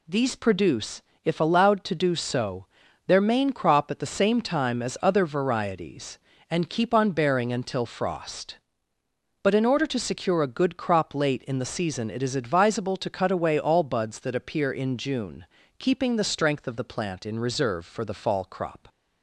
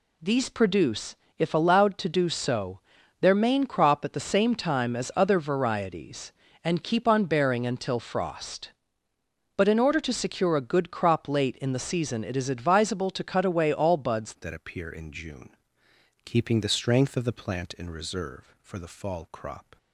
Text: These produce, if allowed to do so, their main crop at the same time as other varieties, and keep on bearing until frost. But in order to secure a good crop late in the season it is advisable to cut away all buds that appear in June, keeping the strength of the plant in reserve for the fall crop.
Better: first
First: none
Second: changes voice at "that"; from 14.4 s on; 5.3 s long

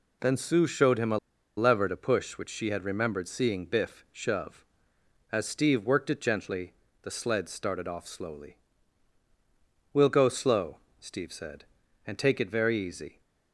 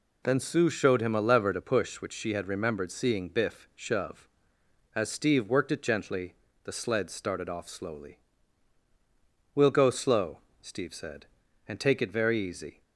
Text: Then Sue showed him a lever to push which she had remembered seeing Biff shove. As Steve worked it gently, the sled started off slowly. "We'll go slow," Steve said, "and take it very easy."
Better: second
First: pauses between "a" and "lever"; at 1.1 s; 0.39 s long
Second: none

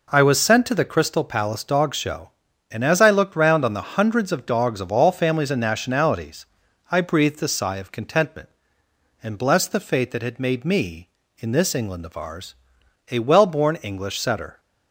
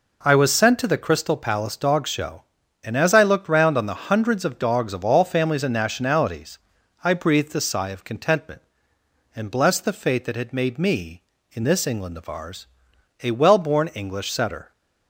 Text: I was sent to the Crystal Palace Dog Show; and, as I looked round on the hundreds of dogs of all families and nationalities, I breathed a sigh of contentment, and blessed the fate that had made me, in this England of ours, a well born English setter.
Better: neither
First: none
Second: none

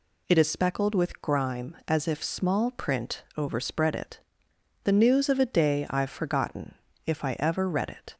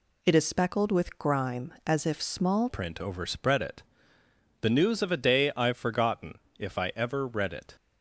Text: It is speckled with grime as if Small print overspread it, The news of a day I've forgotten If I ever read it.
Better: first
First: pauses between "forgotten" and "If"; slight; at 6.7 s; 0.30 s long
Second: changes voice at "print"; from 2.6 s on; 5.1 s long // pauses between "forgotten" and "If"; slight; at 6.3 s; 0.20 s long

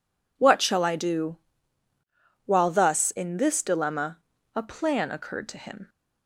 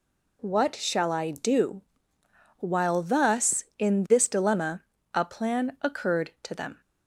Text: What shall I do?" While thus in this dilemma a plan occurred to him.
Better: first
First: pauses between "dilemma" and "a"; at 4.1 s; 0.38 s long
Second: pauses between "dilemma" and "a"; slight; at 4.8 s; 0.32 s long // says "them" for "him"; at 6.5 s

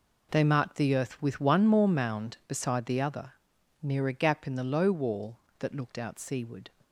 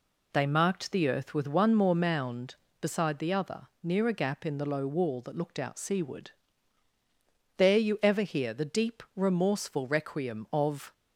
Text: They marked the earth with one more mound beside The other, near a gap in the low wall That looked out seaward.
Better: first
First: none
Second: goes on to say "There you ever hear The deep remorseful requiem of"; strong; from 7.5 s on; 3.3 s long

